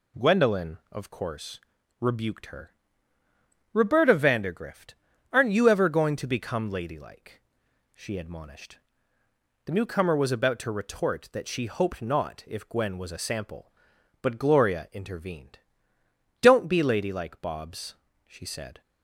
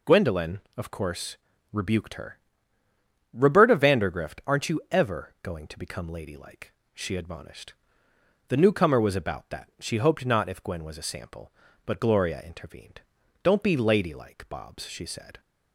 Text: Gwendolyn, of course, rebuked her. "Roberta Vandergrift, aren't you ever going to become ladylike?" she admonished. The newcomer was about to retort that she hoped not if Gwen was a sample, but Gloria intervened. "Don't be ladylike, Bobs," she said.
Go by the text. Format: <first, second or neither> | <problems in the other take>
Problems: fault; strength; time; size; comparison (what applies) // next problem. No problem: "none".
first | skips "to retort"; at 9.4 s